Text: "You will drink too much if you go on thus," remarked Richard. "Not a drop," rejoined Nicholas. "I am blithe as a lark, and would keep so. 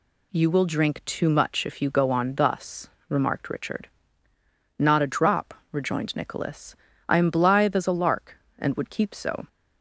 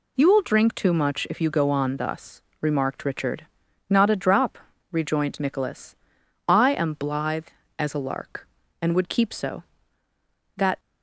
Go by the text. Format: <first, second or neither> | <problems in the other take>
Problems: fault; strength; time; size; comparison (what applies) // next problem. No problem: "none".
first | goes on to say "That"; slight; from 10.5 s on; 0.24 s long